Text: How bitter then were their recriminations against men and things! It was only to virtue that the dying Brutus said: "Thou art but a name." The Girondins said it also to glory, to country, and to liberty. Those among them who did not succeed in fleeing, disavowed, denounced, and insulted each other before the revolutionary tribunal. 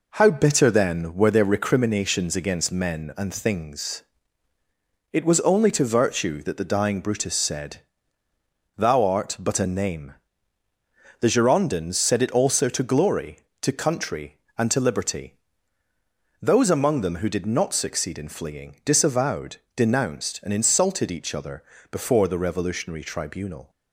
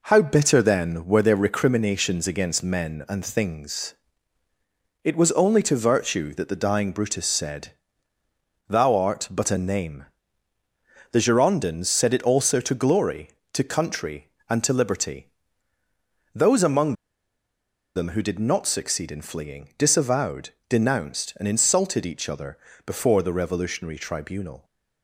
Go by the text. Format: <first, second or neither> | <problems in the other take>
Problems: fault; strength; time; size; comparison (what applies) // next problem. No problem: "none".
first | pauses between "among" and "them"; at 16.9 s; 1.0 s long // pauses between "other" and "before"; slight; at 22.5 s; 0.28 s long; slight in the first